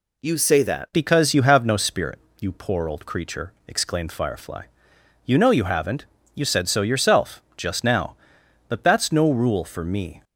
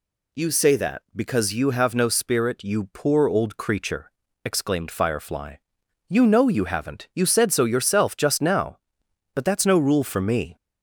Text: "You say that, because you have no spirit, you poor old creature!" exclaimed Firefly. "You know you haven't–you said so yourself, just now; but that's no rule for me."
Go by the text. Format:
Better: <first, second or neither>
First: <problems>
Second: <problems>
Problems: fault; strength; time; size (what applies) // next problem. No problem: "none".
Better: second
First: changes voice at "because"; from 0.9 s on; 9.3 s long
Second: none